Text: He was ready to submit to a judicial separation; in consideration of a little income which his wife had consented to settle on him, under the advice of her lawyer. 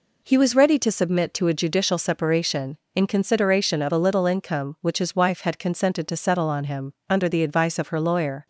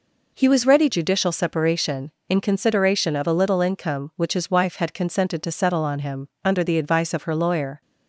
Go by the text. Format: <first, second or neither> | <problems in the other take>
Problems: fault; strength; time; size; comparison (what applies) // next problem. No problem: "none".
first | skips "to submit to a"; at 0.8 s